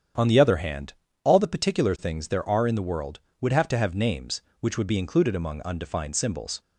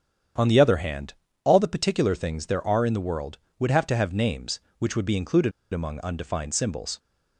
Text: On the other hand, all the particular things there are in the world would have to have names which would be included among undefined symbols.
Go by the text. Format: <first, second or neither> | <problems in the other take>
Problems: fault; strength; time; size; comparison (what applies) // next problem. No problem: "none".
first | starts louder than the rest; strong; until 1.6 s; 8.5 dB; strong in the first // pauses between "included" and "among"; slight; at 5.5 s; 0.23 s long